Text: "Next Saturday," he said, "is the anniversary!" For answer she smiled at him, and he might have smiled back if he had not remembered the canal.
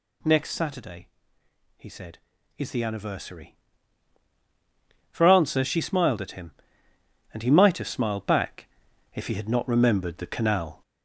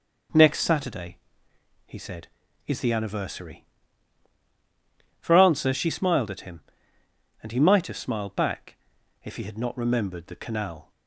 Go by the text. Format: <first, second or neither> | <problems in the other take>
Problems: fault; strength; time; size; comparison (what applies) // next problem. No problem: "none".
second | gets louder; noticeable; throughout; 4.5 dB // pauses between "back" and "if"; noticeable; at 8.6 s; 0.48 s long; noticeable in the second